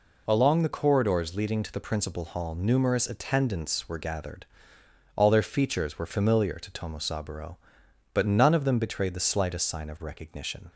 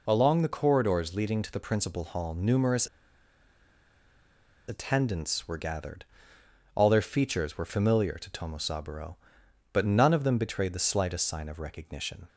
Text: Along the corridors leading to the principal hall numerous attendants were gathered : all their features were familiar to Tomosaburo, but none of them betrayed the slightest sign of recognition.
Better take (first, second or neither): first